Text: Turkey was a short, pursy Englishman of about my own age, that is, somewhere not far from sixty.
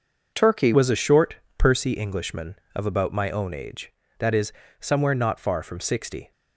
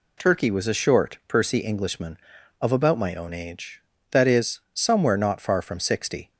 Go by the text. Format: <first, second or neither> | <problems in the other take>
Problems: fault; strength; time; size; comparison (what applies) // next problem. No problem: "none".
second | changes voice at "was"; from 0.7 s on; 5.6 s long